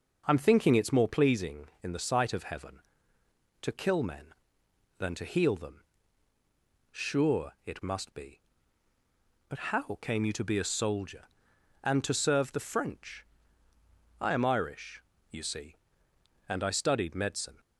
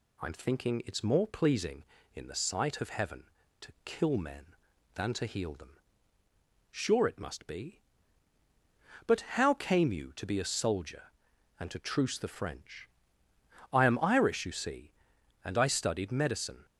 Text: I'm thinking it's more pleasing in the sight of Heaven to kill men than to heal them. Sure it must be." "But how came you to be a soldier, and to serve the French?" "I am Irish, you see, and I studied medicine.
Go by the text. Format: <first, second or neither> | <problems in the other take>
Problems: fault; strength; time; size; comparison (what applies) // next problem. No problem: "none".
first | pauses between "But" and "how"; slight; at 9.2 s; 0.18 s long // says "truce" for "serve"; at 11.7 s